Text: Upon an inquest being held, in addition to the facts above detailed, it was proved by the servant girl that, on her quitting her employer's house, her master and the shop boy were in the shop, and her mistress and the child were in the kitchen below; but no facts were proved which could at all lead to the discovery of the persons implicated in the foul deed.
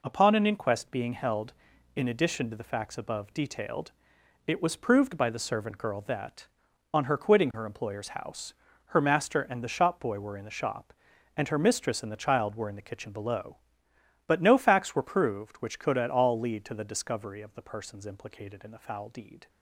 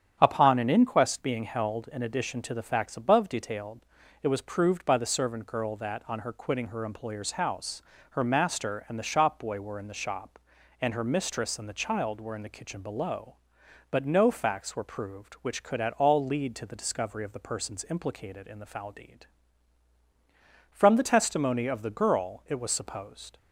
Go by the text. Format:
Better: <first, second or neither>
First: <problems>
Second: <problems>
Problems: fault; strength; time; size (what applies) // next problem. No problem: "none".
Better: first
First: none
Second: starts louder than the rest; strong; until 1.2 s; 9 dB // goes on to say "From the testimony of the girl it was supposed"; strong; from 20.7 s on; 2.6 s long